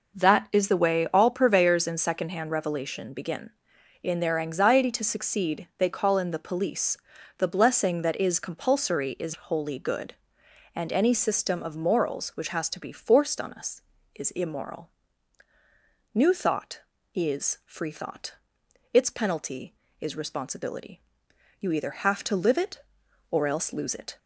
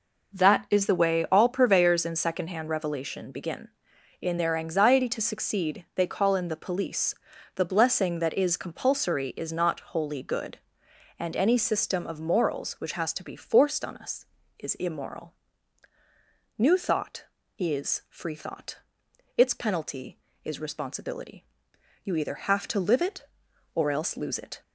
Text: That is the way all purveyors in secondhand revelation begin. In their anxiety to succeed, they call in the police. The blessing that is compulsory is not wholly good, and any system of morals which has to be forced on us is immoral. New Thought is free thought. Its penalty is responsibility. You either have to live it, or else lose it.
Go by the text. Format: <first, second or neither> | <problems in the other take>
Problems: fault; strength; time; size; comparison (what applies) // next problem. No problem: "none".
second | skips "not"; at 9.3 s